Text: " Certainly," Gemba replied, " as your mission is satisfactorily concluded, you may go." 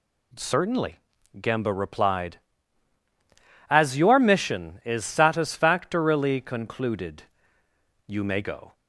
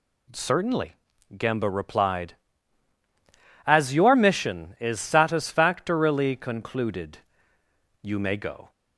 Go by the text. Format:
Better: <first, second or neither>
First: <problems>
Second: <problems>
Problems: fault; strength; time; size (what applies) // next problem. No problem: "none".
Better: neither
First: none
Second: none